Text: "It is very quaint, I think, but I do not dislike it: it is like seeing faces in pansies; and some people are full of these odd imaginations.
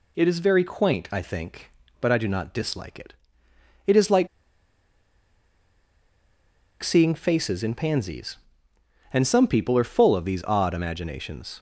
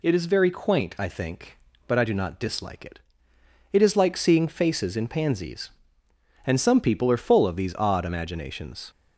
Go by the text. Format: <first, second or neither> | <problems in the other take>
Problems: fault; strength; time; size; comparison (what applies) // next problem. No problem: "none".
second | pauses between "like" and "seeing"; strong; at 4.2 s; 2.5 s long